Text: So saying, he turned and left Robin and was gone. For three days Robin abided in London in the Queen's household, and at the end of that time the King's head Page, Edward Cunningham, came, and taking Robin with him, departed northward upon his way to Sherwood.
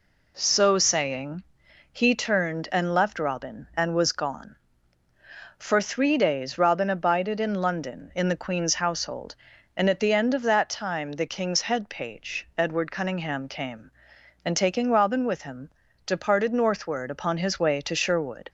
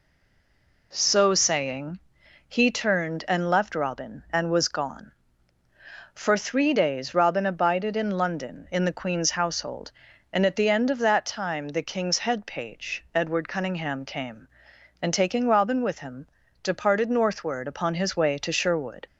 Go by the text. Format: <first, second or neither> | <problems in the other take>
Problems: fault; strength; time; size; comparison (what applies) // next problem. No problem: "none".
first | stays silent before the first word; slight; until 0.9 s; 0.9 s long